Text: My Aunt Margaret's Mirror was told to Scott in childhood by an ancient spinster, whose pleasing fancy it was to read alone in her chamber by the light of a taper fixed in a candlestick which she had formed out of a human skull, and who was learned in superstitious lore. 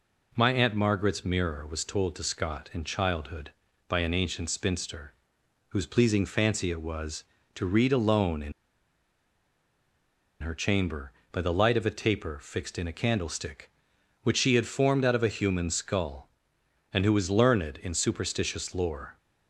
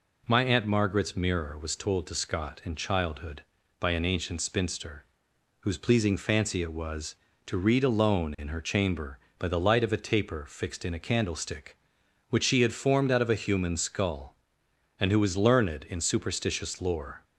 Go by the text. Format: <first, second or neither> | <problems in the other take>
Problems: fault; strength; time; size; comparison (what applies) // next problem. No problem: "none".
second | pauses between "in" and "her"; strong; at 8.5 s; 1.8 s long